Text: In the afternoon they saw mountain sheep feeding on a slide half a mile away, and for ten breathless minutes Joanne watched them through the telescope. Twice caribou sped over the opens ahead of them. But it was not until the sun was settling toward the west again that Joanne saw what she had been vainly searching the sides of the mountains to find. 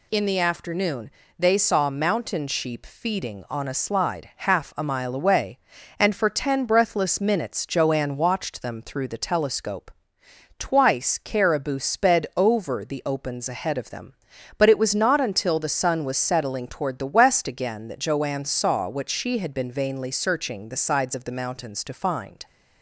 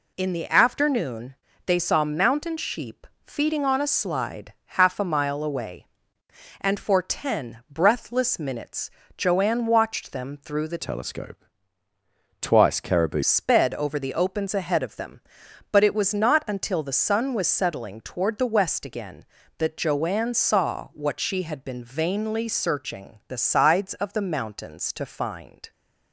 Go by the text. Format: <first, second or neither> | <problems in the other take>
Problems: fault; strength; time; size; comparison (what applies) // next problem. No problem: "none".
first | pauses between "afternoon" and "they"; slight; at 1.3 s; 0.32 s long; slight in the first // pauses between "sheep" and "feeding"; slight; at 3.0 s; 0.16 s long // pauses between "slide" and "half"; slight; at 4.5 s; 0.24 s long // pauses between "minutes" and "Joanne"; slight; at 8.9 s; 0.26 s long // changes voice from "telescope" to "caribou"; from 10.7 to 13.2 s; 2.5 s long